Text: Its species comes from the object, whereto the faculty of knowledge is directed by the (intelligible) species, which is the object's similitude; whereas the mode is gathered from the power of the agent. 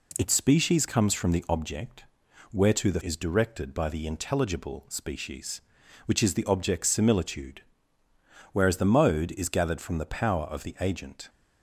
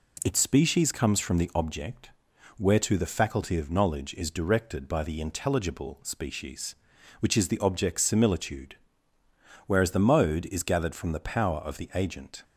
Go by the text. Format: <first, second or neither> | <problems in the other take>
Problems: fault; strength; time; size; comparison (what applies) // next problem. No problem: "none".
second | skips "faculty of knowledge"; at 3.0 s